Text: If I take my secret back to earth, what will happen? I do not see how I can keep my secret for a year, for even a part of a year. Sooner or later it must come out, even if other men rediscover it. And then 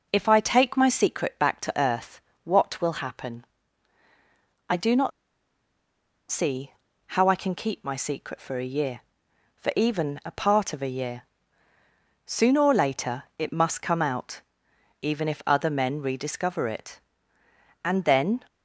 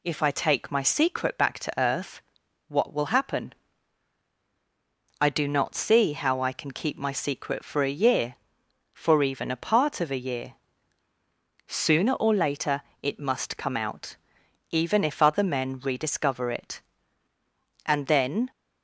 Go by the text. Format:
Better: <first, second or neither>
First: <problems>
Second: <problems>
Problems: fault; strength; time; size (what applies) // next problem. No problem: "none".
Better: second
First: pauses between "not" and "see"; at 5.1 s; 1.1 s long // pauses between "see" and "how"; slight; at 6.7 s; 0.36 s long // pauses between "later" and "it"; slight; at 13.2 s; 0.16 s long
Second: pauses between "later" and "it"; slight; at 12.8 s; 0.22 s long